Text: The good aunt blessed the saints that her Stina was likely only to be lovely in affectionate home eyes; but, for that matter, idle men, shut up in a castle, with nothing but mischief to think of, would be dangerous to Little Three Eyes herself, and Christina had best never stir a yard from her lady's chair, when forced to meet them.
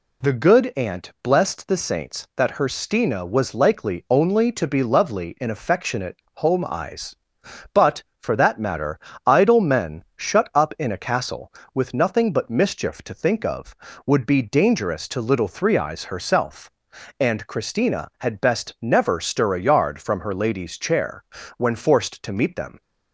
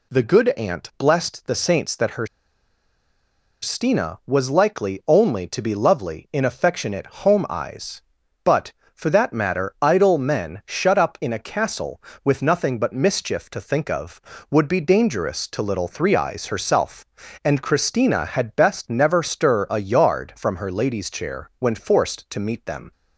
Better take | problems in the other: first | pauses between "her" and "Stina"; strong; at 2.2 s; 1.3 s long // pauses between "affectionate" and "home"; slight; at 7.0 s; 0.18 s long; slight in the first

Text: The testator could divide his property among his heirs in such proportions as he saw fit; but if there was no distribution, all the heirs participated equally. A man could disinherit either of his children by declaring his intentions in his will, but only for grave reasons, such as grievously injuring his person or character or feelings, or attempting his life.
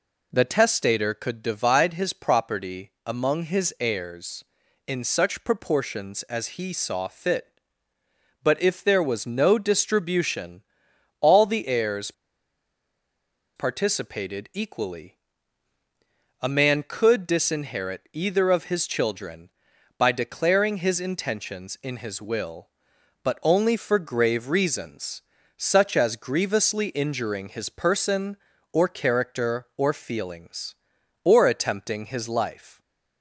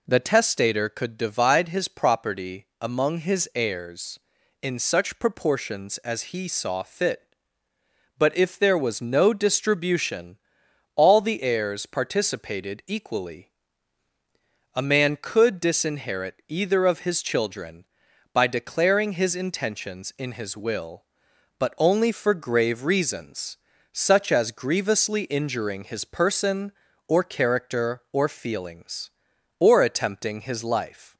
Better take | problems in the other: second | pauses between "heirs" and "participated"; strong; at 12.1 s; 1.4 s long

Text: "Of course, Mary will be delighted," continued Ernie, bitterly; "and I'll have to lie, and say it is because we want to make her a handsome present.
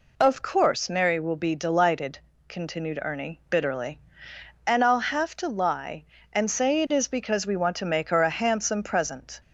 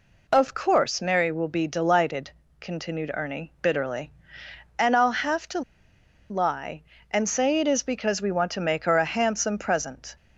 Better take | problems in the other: first | pauses between "to" and "lie"; noticeable; at 5.6 s; 0.68 s long

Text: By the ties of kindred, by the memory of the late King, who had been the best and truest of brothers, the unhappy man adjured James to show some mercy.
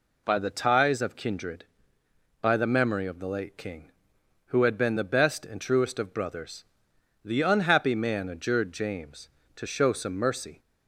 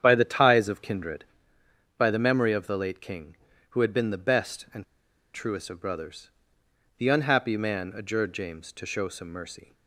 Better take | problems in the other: first | starts louder than the rest; strong; until 1.0 s; 9 dB // pauses between "and" and "truest"; noticeable; at 4.8 s; 0.52 s long

